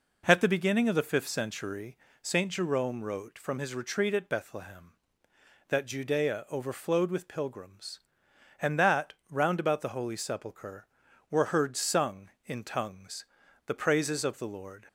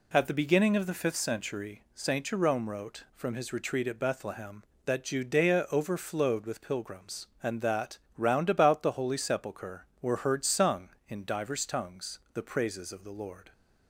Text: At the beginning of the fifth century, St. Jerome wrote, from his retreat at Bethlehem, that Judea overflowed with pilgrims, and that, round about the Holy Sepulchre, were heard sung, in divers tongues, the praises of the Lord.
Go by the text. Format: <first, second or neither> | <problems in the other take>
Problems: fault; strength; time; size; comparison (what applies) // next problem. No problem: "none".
second | skips "divers"; at 12.6 s